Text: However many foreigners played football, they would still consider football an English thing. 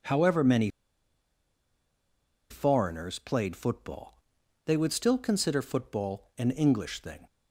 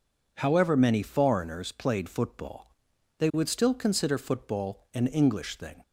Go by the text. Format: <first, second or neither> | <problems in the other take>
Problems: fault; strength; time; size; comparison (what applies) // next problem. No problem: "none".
second | pauses between "many" and "foreigners"; strong; at 0.6 s; 1.8 s long